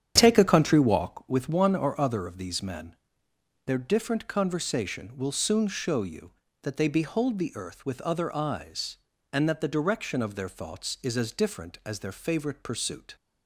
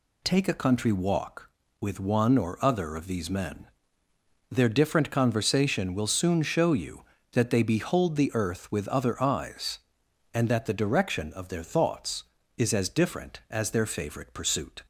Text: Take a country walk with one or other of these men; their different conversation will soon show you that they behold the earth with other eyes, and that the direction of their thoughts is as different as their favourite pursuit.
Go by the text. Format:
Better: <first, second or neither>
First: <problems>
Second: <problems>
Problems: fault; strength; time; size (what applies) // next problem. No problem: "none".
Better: second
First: starts louder than the rest; strong; until 1.3 s; 9.5 dB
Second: none